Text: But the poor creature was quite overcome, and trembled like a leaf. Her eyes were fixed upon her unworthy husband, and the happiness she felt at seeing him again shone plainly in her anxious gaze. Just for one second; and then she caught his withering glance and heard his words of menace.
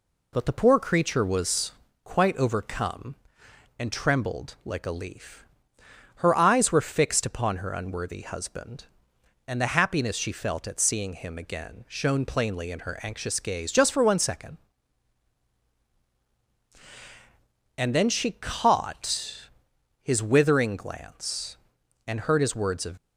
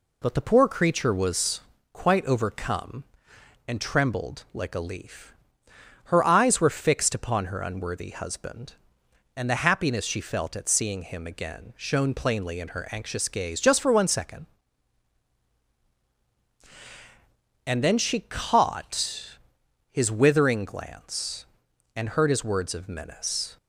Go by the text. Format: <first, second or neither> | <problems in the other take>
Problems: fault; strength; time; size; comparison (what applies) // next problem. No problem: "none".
second | pauses between "was" and "quite"; slight; at 1.6 s; 0.32 s long; slight in the second // pauses between "caught" and "his"; noticeable; at 19.4 s; 0.54 s long; noticeable in the second // stops before "menace"; at 22.9 s